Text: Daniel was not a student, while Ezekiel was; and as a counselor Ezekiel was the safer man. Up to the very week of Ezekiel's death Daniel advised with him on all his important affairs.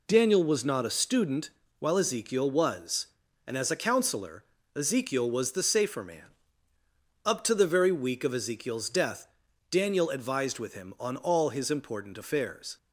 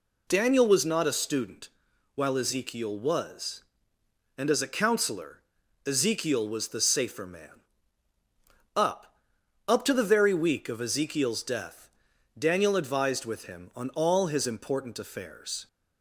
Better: first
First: pauses between "counselor" and "Ezekiel"; slight; at 4.4 s; 0.28 s long // pauses between "death" and "Daniel"; at 9.2 s; 0.42 s long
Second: pauses between "counselor" and "Ezekiel"; noticeable; at 5.3 s; 0.46 s long // says "Up" twice; at 9.6 s // pauses between "death" and "Daniel"; noticeable; at 11.8 s; 0.48 s long

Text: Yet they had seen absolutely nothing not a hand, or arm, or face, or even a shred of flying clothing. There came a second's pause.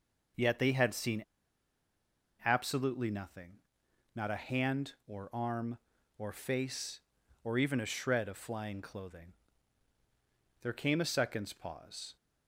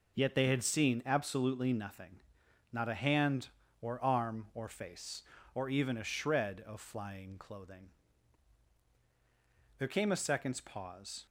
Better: second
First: starts louder than the rest; until 2.5 s; 6.5 dB // pauses between "seen" and "absolutely"; at 1.2 s; 1.2 s long // pauses between "nothing" and "not"; noticeable; at 3.5 s; 0.64 s long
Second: pauses between "nothing" and "not"; noticeable; at 2.2 s; 0.50 s long

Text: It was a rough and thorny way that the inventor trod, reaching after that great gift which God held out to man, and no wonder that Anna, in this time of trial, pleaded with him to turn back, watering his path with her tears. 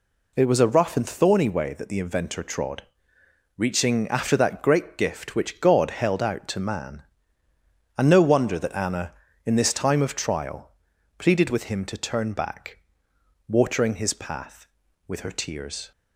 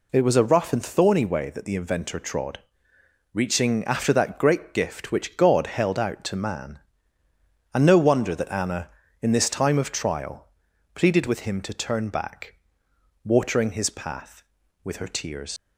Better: first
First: none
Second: leaves "tears" unfinished; at 15.5 s; 110 ms

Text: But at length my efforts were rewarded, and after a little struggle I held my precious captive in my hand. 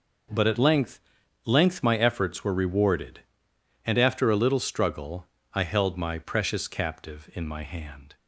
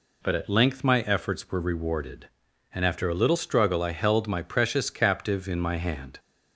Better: second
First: says "length" twice; at 1.4 s // pauses between "struggle" and "I"; slight; at 5.2 s; 0.28 s long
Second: none

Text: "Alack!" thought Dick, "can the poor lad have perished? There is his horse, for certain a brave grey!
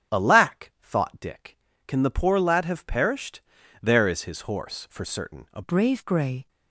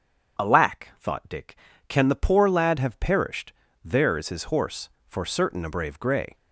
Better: second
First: starts louder than the rest; strong; until 1.2 s; 9.5 dB // changes voice at "brave"; from 5.6 s on; 0.8 s long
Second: starts louder than the rest; strong; until 1.5 s; 7.5 dB

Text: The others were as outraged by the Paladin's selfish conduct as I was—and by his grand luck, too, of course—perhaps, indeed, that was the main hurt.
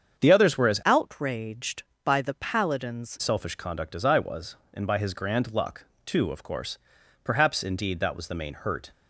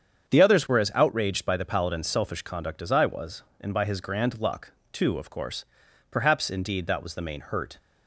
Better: second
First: starts louder than the rest; strong; until 1.2 s; 7.5 dB // changes voice from "outraged" to "Paladin's"; from 0.8 to 3.1 s; 2.3 s long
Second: starts louder than the rest; strong; until 1.3 s; 7.5 dB

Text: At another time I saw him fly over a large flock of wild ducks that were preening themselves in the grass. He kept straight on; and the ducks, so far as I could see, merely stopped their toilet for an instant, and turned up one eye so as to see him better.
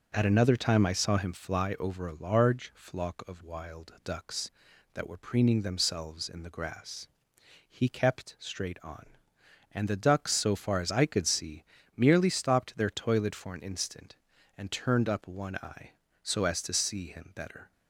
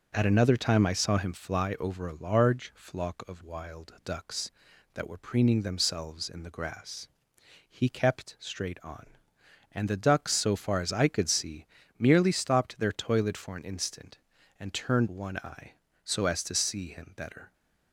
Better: first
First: none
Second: skips "up"; at 15.0 s

